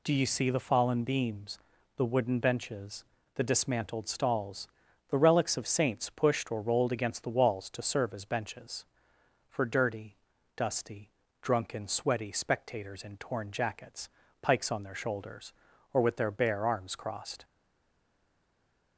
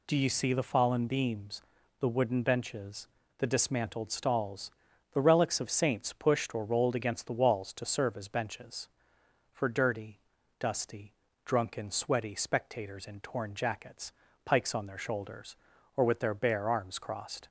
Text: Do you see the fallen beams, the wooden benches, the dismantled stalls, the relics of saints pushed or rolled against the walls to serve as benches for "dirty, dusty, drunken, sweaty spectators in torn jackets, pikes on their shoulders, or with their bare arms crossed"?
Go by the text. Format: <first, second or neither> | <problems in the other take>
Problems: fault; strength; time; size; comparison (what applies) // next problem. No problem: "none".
second | stays silent after the last word; noticeable; from 17.4 s on; 1.5 s long